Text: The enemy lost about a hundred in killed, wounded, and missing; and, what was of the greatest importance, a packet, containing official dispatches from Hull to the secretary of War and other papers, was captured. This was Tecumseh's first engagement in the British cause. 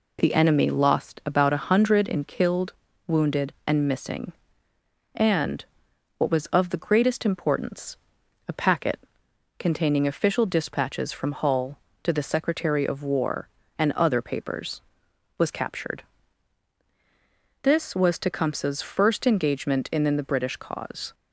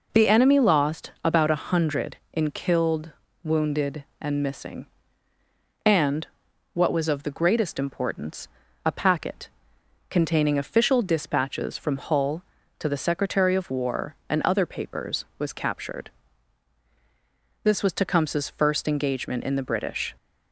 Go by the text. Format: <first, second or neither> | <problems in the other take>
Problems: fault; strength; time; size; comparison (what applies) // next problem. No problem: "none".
first | stops before "cause"; at 20.1 s